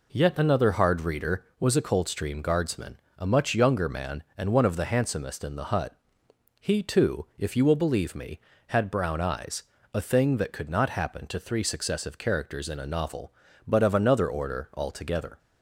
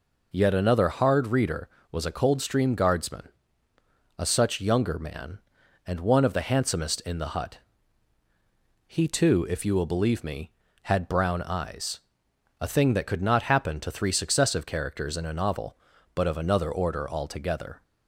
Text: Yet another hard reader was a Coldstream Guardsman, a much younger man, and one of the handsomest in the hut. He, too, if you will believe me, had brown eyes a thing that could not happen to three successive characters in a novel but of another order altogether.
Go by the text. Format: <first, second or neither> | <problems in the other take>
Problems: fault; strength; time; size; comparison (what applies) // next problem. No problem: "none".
first | says "such" for "much"; at 4.2 s // pauses between "eyes" and "a"; noticeable; at 12.0 s; 0.60 s long; slight in the first